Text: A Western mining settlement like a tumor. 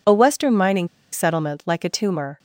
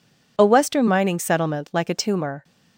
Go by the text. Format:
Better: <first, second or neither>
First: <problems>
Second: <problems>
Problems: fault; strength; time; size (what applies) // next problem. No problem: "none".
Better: second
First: pauses between "mining" and "settlement"; slight; at 0.8 s; 0.24 s long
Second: none